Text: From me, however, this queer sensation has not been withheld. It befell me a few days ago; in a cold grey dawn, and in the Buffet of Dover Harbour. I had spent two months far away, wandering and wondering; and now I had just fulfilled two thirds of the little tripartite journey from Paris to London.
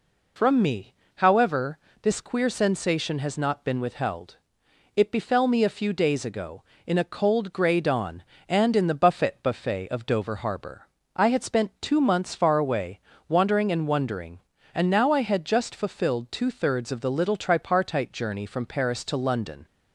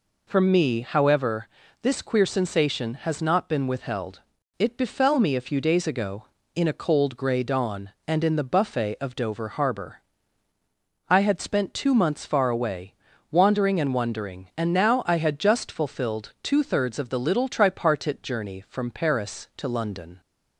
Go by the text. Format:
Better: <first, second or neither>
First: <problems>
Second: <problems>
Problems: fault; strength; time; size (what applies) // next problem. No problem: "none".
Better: second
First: says "Buffet" twice; at 9.4 s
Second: none